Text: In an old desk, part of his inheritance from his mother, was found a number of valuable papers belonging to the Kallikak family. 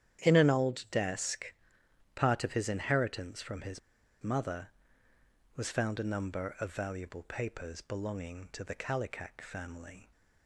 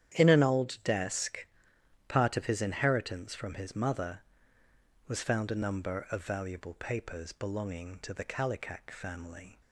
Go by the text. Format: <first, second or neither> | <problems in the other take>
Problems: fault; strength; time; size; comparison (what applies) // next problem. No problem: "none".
second | starts louder than the rest; strong; until 1.2 s; 10 dB; strong in the second // pauses between "his" and "mother"; at 3.7 s; 0.43 s long